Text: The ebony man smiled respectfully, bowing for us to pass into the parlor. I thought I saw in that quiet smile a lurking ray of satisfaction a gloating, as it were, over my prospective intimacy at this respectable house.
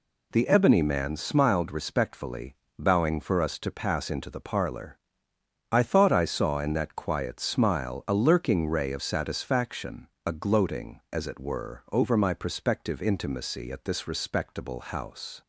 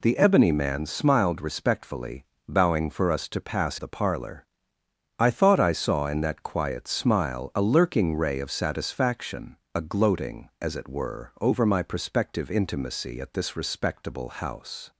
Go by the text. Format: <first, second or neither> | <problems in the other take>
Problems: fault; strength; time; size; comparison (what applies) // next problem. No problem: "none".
first | skips "into"; at 3.7 s // pauses between "satisfaction" and "a"; slight; at 9.5 s; 0.18 s long; slight in the first